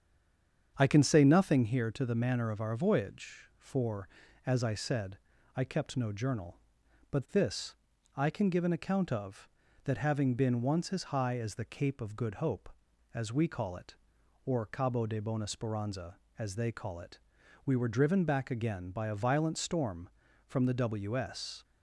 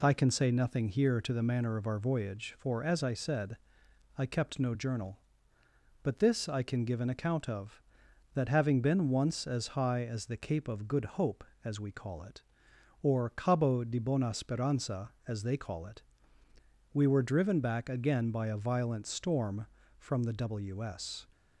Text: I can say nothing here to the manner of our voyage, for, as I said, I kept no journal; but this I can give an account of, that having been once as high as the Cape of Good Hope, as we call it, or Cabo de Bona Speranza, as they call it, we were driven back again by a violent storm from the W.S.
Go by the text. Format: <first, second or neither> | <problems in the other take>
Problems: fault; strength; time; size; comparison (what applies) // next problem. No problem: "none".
second | stays silent before the first word; slight; until 0.7 s; 0.7 s long // starts louder than the rest; strong; until 1.7 s; 7.5 dB // pauses between "this" and "I"; at 7.7 s; 0.40 s long